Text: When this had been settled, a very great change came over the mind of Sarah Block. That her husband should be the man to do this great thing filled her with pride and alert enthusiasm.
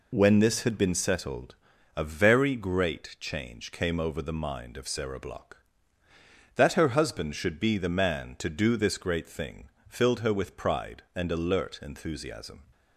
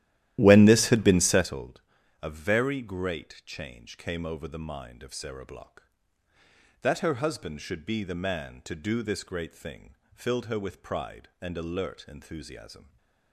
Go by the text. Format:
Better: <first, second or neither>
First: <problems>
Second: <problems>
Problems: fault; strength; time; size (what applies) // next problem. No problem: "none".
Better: first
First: pauses between "thing" and "filled"; slight; at 9.6 s; 0.18 s long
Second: starts louder than the rest; strong; until 1.7 s; 13.5 dB // pauses between "thing" and "filled"; slight; at 9.9 s; 0.18 s long